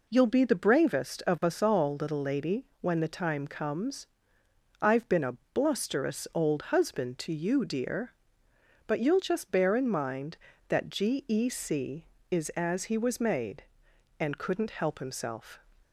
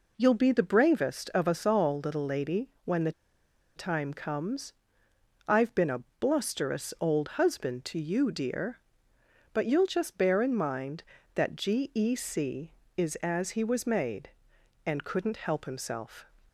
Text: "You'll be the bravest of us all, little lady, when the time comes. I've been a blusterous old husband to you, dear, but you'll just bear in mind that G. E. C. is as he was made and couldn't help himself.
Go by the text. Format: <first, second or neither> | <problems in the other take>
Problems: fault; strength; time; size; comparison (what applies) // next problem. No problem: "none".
first | pauses between "the" and "time"; noticeable; at 3.1 s; 0.65 s long // pauses between "a" and "blusterous"; slight; at 6.0 s; 0.16 s long; slight in the first